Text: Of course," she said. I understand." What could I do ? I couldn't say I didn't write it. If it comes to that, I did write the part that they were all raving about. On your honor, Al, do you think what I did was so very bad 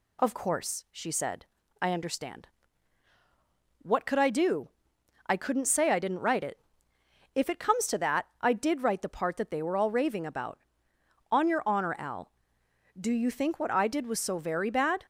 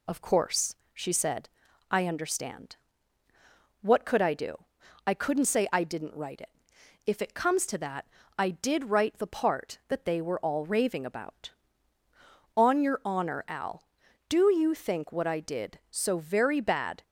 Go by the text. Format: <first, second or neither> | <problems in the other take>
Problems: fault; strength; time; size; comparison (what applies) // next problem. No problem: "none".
first | skips "was"; at 15.8 s